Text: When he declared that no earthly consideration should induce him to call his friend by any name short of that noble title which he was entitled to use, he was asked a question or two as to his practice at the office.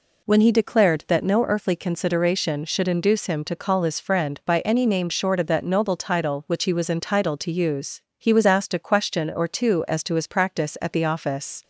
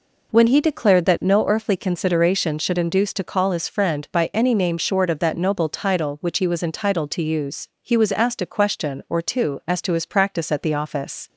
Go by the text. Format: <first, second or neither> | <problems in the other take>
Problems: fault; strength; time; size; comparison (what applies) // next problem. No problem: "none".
first | skips "him"; at 3.1 s